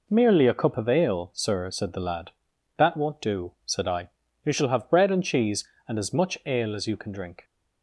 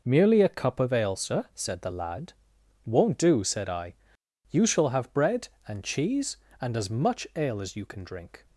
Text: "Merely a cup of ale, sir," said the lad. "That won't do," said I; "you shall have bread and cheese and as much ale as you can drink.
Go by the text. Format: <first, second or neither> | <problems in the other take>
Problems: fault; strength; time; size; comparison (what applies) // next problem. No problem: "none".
first | skips "That"; at 2.5 s